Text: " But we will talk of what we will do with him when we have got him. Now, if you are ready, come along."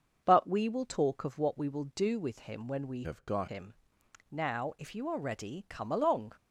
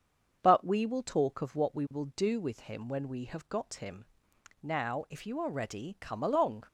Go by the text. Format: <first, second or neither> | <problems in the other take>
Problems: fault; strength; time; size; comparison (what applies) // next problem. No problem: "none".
second | starts louder than the rest; until 1.2 s; 6.5 dB; also in the second // changes voice from "have" to "got"; from 3.0 to 3.4 s; 0.4 s long